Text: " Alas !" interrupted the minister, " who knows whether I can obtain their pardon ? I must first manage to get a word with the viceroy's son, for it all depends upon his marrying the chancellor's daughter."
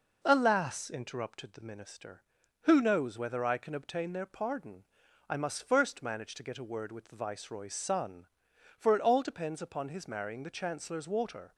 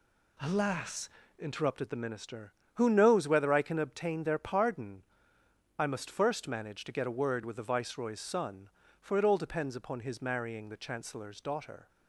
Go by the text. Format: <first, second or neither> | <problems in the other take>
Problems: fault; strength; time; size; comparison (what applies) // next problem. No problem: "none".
second | says "water" for "daughter"; at 11.0 s